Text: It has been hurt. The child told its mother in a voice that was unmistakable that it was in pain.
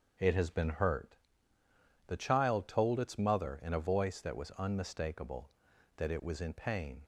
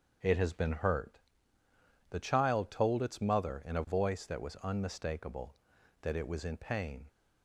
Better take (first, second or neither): neither